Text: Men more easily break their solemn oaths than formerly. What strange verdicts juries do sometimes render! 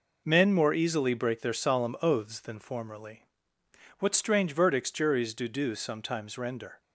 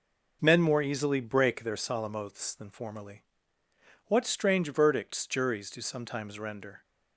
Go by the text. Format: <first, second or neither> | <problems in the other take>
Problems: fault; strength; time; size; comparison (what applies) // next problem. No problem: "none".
second | says "do" twice; at 5.4 s